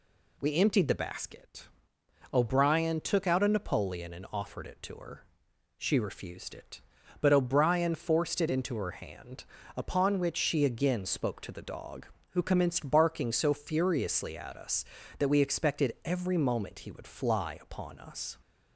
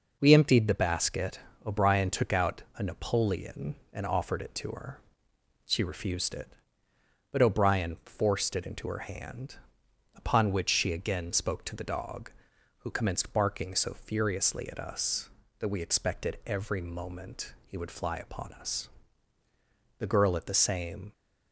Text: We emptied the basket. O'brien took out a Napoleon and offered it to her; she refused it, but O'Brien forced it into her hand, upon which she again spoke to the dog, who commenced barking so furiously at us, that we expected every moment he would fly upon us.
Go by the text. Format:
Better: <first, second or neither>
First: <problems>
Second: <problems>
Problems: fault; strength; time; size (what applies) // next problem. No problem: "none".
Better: first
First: none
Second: goes on to say "The girl at the same"; noticeable; from 19.9 s on; 1.1 s long